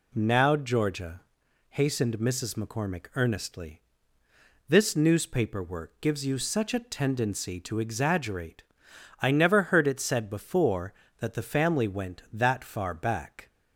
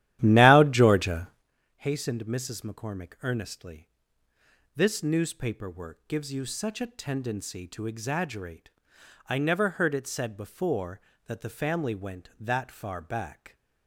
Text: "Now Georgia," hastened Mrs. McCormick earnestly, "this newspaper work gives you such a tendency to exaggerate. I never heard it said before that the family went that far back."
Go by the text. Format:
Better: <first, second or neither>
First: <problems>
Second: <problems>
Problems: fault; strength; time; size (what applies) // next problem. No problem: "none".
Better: first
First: none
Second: starts louder than the rest; strong; until 1.5 s; 13 dB